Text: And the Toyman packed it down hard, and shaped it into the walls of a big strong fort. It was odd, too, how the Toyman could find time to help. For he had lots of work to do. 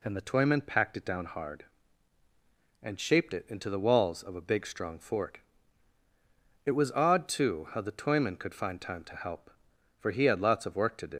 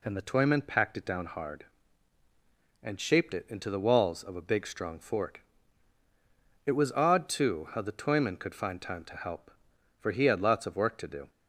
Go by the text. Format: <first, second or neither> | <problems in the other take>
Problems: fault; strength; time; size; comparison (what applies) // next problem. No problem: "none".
second | leaves "do" unfinished; at 11.1 s; 105 ms